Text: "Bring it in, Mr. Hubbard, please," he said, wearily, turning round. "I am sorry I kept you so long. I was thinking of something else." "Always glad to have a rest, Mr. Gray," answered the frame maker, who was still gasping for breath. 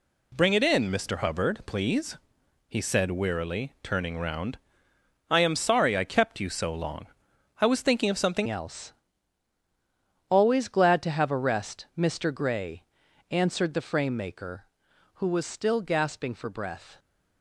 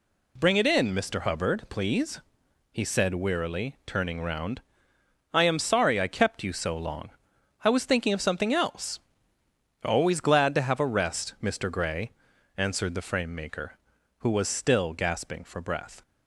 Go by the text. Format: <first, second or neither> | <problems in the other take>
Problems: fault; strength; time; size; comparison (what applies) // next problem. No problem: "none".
second | changes voice at "else"; from 8.4 s on; 8.5 s long